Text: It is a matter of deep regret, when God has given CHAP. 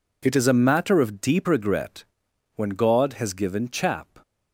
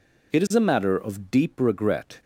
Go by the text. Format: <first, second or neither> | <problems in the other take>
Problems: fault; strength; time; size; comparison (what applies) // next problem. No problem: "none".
first | stops before "when God has given CHAP"; at 2.2 s